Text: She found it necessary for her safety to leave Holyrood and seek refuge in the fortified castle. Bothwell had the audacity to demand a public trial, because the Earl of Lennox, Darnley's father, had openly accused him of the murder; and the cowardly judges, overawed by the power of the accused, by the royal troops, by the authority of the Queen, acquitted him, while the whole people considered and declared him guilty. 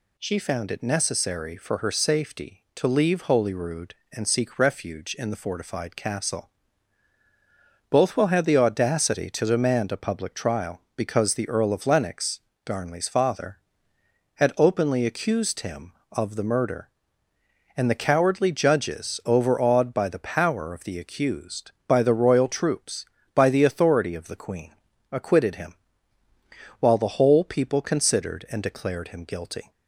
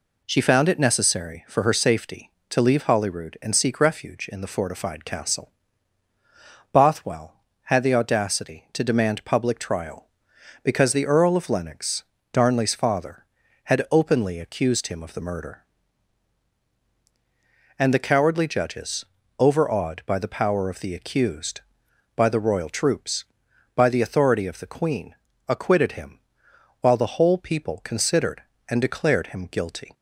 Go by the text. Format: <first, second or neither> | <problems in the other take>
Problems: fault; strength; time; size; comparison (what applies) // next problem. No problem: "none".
first | skips "a"; at 9.2 s